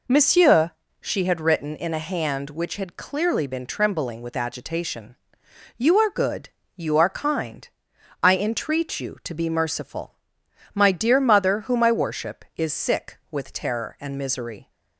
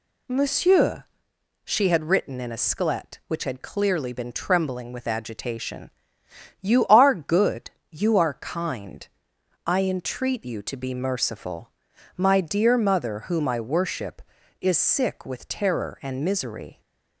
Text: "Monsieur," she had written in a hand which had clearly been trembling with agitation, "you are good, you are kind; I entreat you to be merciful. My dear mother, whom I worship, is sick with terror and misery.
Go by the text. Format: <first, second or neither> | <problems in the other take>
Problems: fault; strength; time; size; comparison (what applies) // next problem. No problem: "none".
first | says "sklet" for "hand"; at 2.5 s